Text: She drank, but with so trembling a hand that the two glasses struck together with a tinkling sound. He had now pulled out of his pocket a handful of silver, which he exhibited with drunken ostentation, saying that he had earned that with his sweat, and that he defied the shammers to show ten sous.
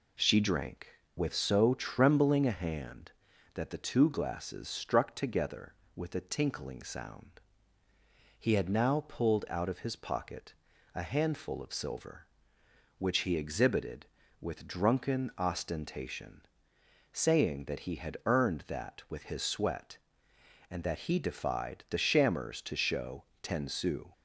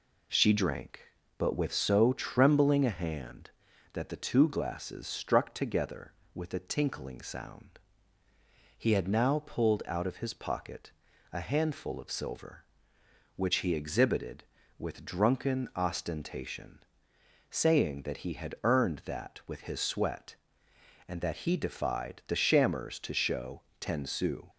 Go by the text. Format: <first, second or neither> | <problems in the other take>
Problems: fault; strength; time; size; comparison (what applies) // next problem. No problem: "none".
second | skips "but"; at 1.0 s // pauses between "pocket" and "a"; at 10.5 s; 0.40 s long; also in the second // pauses between "show" and "ten"; slight; at 23.2 s; 0.18 s long; slight in the second